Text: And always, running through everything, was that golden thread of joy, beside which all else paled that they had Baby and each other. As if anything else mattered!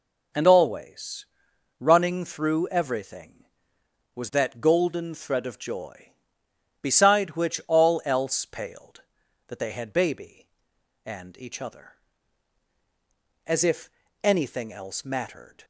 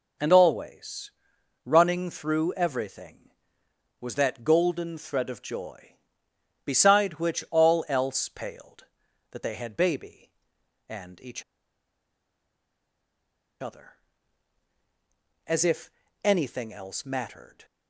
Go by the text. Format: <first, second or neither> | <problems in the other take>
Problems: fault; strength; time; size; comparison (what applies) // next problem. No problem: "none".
first | pauses between "each" and "other"; strong; at 11.4 s; 2.1 s long // pauses between "if" and "anything"; slight; at 15.8 s; 0.34 s long; slight in the first